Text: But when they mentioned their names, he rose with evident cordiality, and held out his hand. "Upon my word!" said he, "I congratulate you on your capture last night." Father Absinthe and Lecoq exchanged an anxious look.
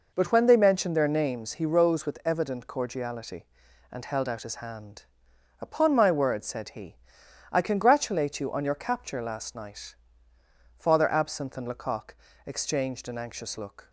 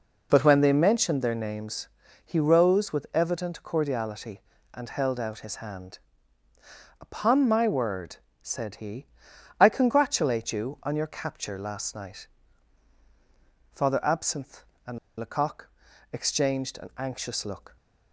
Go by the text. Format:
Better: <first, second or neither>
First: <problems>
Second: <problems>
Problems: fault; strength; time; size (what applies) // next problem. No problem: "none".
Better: first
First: pauses between "Lecoq" and "exchanged"; slight; at 12.1 s; 0.30 s long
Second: pauses between "and" and "Lecoq"; slight; at 14.9 s; 0.21 s long // pauses between "Lecoq" and "exchanged"; at 15.6 s; 0.44 s long